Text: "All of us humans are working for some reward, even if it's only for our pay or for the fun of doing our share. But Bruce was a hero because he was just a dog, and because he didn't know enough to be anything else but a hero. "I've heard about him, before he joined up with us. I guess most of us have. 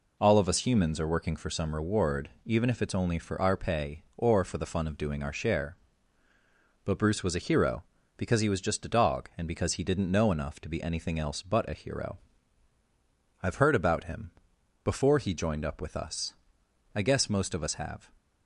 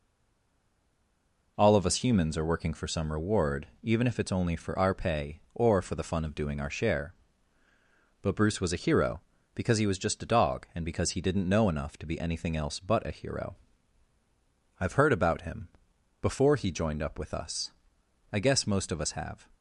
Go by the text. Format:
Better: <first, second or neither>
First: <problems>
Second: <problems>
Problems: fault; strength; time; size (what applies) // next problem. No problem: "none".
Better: first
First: none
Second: stays silent before the first word; noticeable; until 1.5 s; 1.5 s long